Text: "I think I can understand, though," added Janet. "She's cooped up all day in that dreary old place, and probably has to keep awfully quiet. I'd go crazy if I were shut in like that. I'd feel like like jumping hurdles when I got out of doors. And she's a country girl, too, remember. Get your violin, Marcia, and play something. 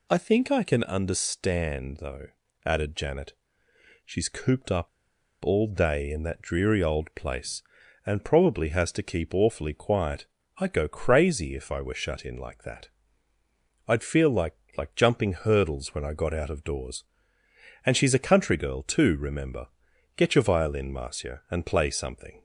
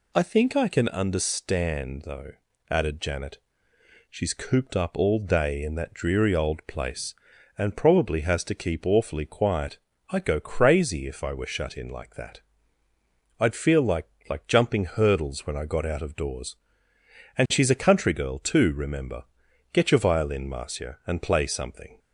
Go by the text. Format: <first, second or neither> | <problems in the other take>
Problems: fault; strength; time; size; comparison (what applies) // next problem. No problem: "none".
second | pauses between "up" and "all"; noticeable; at 4.8 s; 0.55 s long // pauses between "like" and "like"; slight; at 14.5 s; 0.24 s long; slight in the second